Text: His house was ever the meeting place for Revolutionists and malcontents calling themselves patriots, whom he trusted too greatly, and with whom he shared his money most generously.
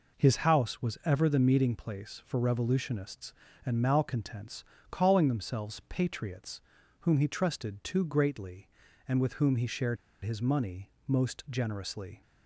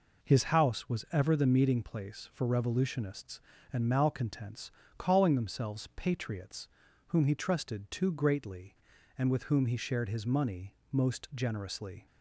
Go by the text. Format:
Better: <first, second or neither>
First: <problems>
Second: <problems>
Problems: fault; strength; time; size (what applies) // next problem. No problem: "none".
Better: second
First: pauses between "malcontents" and "calling"; slight; at 4.6 s; 0.28 s long // pauses between "shared" and "his"; slight; at 9.9 s; 0.26 s long // pauses between "money" and "most"; slight; at 10.8 s; 0.18 s long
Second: pauses between "malcontents" and "calling"; slight; at 4.7 s; 0.28 s long // pauses between "money" and "most"; slight; at 10.7 s; 0.18 s long